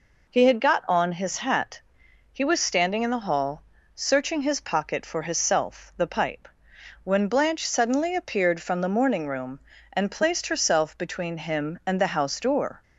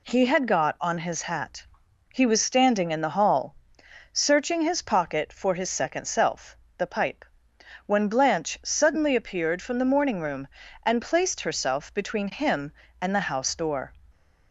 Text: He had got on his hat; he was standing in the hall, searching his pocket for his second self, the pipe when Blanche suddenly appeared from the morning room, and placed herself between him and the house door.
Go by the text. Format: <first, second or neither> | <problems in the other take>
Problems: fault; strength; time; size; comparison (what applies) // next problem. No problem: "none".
second | skips "second"; at 5.3 s // pauses between "pipe" and "when"; noticeable; at 6.4 s; 0.56 s long; noticeable in the second